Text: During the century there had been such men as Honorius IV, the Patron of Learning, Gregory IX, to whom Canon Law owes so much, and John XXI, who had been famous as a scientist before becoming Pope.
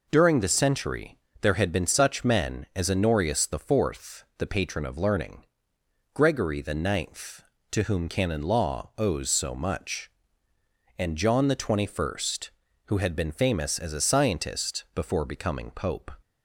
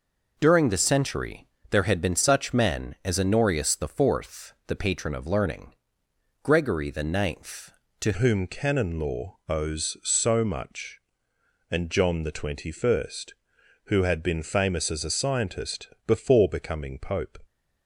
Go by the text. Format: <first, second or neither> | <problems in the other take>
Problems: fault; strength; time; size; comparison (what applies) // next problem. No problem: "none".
first | pauses between "century" and "there"; slight; at 1.4 s; 0.24 s long; slight in the first // changes voice at "whom"; from 8.1 s on; 9.2 s long // pauses between "scientist" and "before"; slight; at 15.8 s; 0.18 s long